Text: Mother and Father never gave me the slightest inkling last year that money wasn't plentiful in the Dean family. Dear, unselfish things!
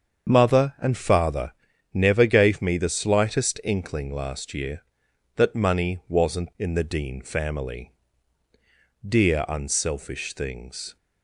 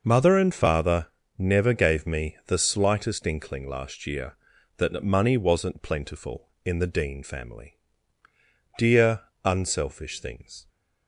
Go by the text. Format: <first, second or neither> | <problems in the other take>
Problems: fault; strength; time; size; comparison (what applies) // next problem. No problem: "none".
second | starts louder than the rest; until 1.3 s; 7 dB // pauses between "Father" and "never"; at 1.5 s; 0.42 s long; slight in the second // skips "plentiful"; at 6.5 s